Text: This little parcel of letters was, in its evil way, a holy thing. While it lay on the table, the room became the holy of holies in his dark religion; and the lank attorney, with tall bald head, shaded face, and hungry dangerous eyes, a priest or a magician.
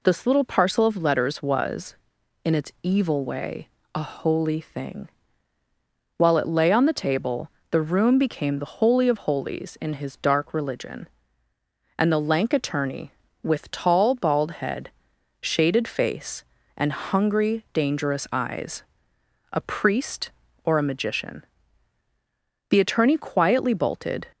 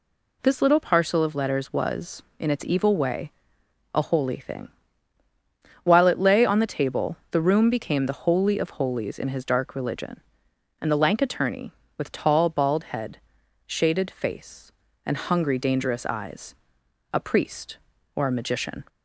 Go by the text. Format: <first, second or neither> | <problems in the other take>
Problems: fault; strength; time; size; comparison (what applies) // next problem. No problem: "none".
second | goes on to say "The attorney quietly bolted"; from 22.6 s on; 1.5 s long